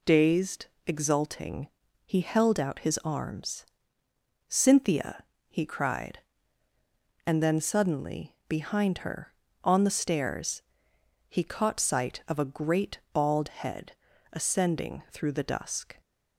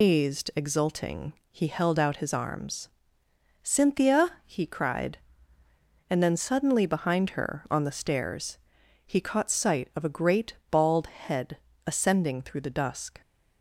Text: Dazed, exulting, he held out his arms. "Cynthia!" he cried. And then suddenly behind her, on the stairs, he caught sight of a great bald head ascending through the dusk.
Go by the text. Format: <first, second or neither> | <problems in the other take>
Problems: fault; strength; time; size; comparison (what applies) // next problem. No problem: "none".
first | loses the start of "Dazed"; at 0.0 s; 155 ms // pauses between "great" and "bald"; slight; at 10.5 s; 0.16 s long // pauses between "head" and "ascending"; slight; at 11.5 s; 0.30 s long; also in the first